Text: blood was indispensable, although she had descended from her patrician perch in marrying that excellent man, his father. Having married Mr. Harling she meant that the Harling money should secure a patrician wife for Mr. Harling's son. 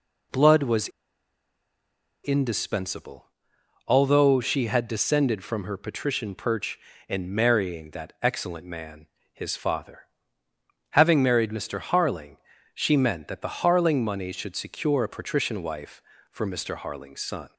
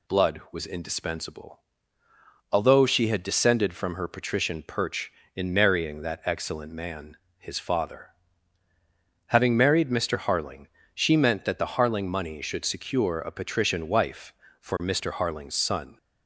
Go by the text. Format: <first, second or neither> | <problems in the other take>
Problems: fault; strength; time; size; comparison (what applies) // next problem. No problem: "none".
second | pauses between "was" and "indispensable"; strong; at 0.8 s; 1.3 s long // pauses between "Harling" and "she"; at 12.3 s; 0.38 s long; slight in the second